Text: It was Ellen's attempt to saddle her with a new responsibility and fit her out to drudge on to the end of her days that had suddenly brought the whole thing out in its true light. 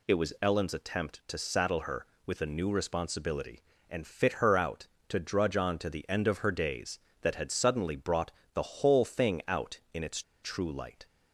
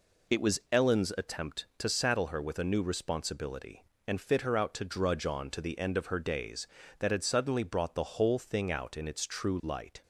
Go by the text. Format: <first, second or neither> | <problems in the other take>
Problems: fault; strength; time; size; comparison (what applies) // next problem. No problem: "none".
second | pauses between "brought" and "the"; slight; at 8.3 s; 0.22 s long // pauses between "its" and "true"; slight; at 10.2 s; 0.21 s long